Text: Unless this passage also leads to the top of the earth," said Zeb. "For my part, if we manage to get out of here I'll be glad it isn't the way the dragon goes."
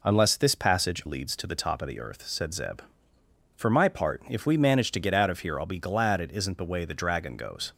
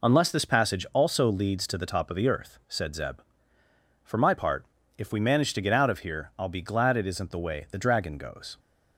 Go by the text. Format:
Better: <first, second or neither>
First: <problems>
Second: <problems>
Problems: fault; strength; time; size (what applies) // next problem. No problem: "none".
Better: second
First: skips "also"; at 1.0 s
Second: none